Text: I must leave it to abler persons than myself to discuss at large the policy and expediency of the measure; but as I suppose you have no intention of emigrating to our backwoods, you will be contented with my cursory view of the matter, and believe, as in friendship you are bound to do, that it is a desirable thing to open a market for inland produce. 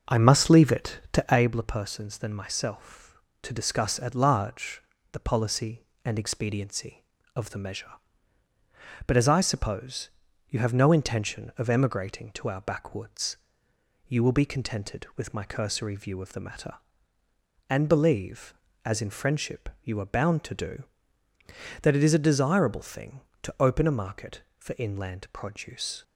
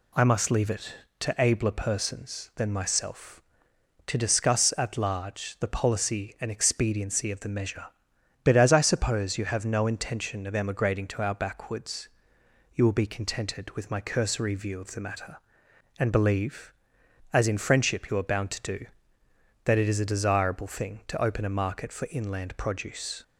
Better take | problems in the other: second | starts louder than the rest; noticeable; until 1.5 s; 5.5 dB // pauses between "large" and "the"; slight; at 4.8 s; 0.32 s long // pauses between "suppose" and "you"; at 10.0 s; 0.40 s long // pauses between "friendship" and "you"; slight; at 19.6 s; 0.16 s long

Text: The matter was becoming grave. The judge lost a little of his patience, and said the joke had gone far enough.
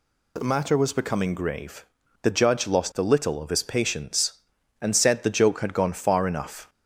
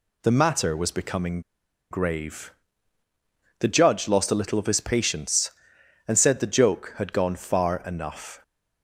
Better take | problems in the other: first | pauses between "becoming" and "grave"; noticeable; at 1.4 s; 0.50 s long

